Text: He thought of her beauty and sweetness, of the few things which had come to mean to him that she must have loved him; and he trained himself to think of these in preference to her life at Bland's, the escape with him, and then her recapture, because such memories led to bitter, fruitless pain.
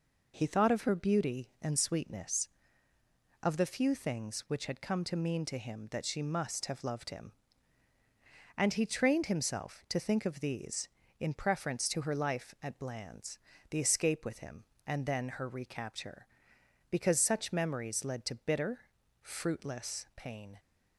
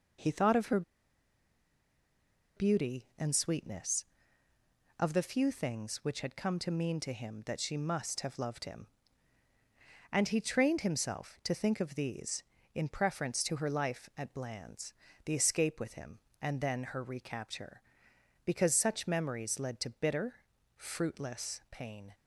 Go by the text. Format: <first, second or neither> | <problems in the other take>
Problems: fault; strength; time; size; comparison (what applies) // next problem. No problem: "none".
first | pauses between "her" and "beauty"; strong; at 0.8 s; 1.7 s long